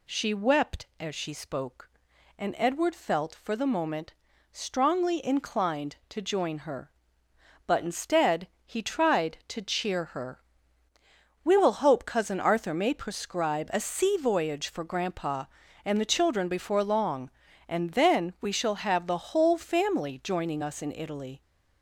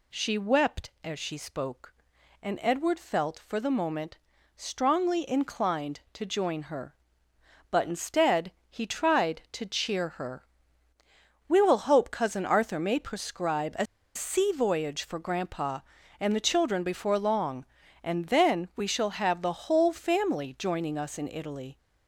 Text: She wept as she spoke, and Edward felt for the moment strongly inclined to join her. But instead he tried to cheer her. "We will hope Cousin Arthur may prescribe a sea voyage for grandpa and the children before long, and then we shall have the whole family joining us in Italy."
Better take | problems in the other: first | pauses between "moment" and "strongly"; at 4.1 s; 0.40 s long; also in the first // pauses between "instead" and "he"; slight; at 8.5 s; 0.18 s long; slight in the first // pauses between "a" and "sea"; slight; at 13.8 s; 0.29 s long

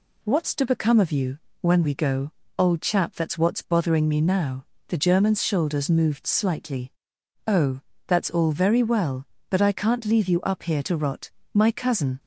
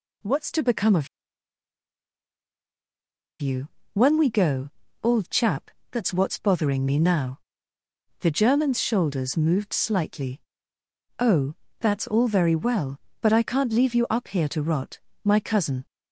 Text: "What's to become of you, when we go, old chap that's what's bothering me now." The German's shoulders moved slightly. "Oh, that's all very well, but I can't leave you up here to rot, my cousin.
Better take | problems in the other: first | pauses between "of" and "you"; strong; at 1.0 s; 2.3 s long // pauses between "chap" and "that's"; slight; at 5.7 s; 0.20 s long

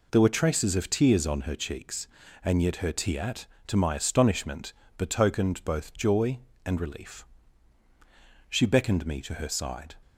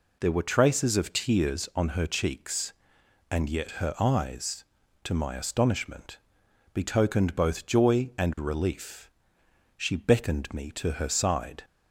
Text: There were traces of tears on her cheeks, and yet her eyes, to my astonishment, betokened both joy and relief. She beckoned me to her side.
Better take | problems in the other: second | says "tiat" for "eyes"; at 2.9 s

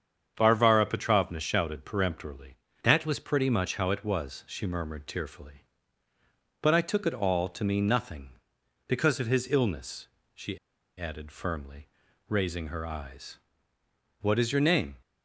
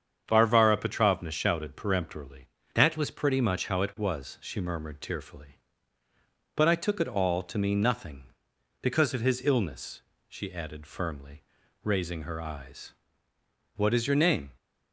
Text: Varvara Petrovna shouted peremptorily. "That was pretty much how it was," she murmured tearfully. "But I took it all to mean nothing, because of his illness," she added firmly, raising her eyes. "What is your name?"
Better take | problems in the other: second | starts louder than the rest; strong; until 1.3 s; 7.5 dB; strong in the second // pauses between "she" and "added"; at 10.5 s; 0.39 s long

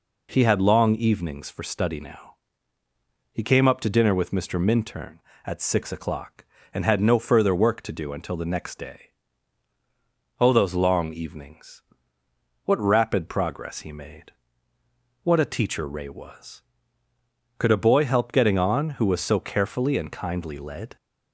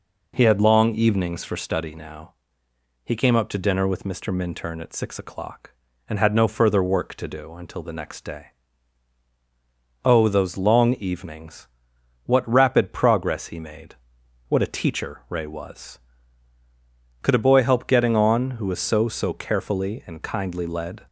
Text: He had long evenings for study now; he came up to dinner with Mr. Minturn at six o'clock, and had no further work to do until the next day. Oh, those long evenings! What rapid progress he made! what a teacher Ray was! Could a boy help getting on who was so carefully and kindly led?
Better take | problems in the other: first | says "so" twice; at 19.0 s

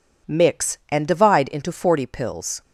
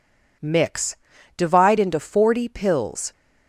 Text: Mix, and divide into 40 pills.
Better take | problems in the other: first | skips "and"; at 1.1 s

